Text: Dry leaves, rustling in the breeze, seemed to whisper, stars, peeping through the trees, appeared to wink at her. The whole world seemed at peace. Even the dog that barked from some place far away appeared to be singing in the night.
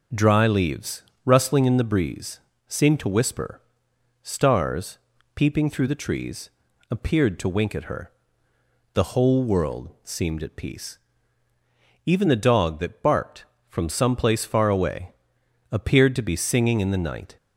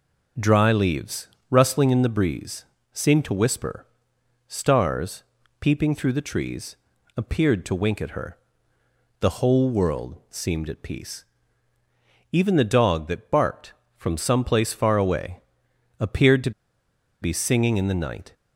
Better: first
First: pauses between "away" and "appeared"; noticeable; at 15.1 s; 0.60 s long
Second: pauses between "away" and "appeared"; noticeable; at 15.3 s; 0.60 s long // pauses between "to" and "be"; noticeable; at 16.5 s; 0.71 s long

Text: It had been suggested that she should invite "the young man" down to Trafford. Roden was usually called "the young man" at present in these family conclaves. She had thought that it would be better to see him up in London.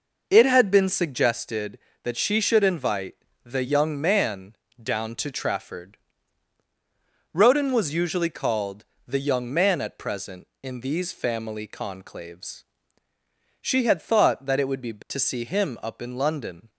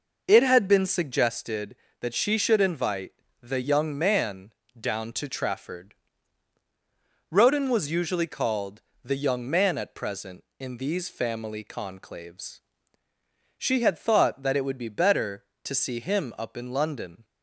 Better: second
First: pauses between "invite" and "the"; slight; at 3.1 s; 0.30 s long // pauses between "man" and "down"; slight; at 4.5 s; 0.26 s long // pauses between "called" and "the"; slight; at 8.8 s; 0.20 s long // skips "better"; at 15.0 s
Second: pauses between "invite" and "the"; slight; at 3.1 s; 0.30 s long // pauses between "man" and "down"; slight; at 4.5 s; 0.26 s long // pauses between "called" and "the"; slight; at 8.8 s; 0.20 s long

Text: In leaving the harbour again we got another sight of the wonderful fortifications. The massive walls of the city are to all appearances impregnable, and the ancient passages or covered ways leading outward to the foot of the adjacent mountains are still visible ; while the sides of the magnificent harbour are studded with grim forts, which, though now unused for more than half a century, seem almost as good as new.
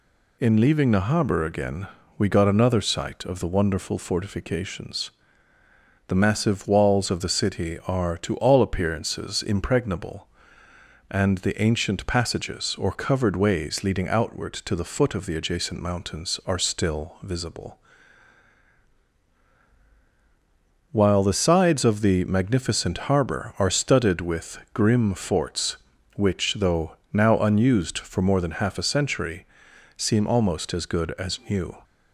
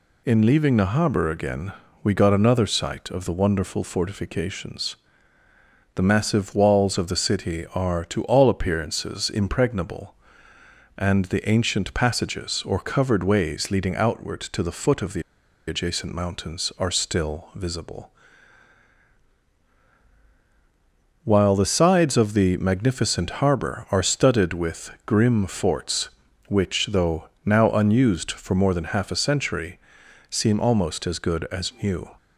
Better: first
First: pauses between "again" and "we"; slight; at 1.8 s; 0.28 s long // pauses between "with" and "grim"; slight; at 24.5 s; 0.16 s long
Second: pauses between "again" and "we"; slight; at 1.7 s; 0.28 s long // pauses between "the" and "adjacent"; noticeable; at 15.2 s; 0.46 s long // pauses between "with" and "grim"; slight; at 24.9 s; 0.16 s long

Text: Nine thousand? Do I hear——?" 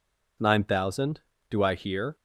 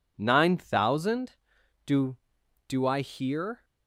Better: first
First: none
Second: says "Do" twice; at 2.6 s

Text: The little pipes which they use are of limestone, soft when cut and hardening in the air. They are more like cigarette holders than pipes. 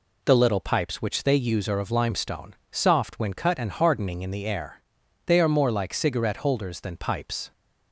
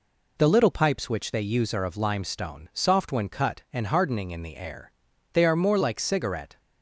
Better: first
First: none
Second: stops before "holders than pipes"; at 6.5 s

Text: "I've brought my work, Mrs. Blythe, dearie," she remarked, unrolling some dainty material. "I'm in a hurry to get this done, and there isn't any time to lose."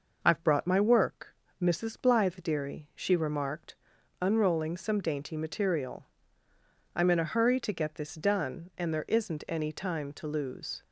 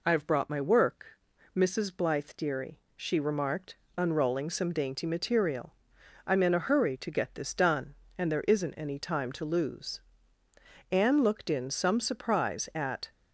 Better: first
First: none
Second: goes on to say "Anne looked in some surprise at"; strong; from 10.9 s on; 2.2 s long

